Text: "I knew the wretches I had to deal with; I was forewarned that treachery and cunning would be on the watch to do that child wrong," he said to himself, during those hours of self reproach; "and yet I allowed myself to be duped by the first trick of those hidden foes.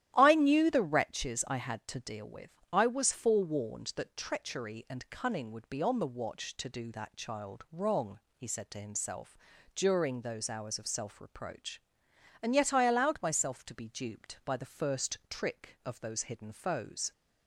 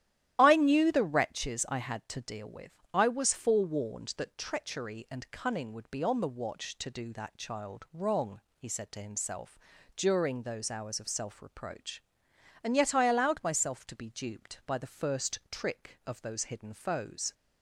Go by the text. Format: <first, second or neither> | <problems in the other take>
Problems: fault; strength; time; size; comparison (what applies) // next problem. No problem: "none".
first | loses the start of "I"; at 0.3 s; 35 ms // starts louder than the rest; strong; until 1.3 s; 12.5 dB; strong in the first